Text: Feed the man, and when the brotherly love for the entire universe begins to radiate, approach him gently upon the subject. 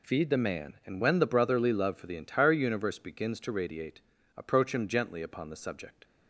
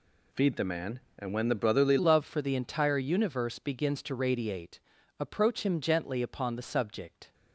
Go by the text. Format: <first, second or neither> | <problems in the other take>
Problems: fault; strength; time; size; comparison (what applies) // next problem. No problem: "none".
first | changes voice at "love"; from 1.9 s on; 5.4 s long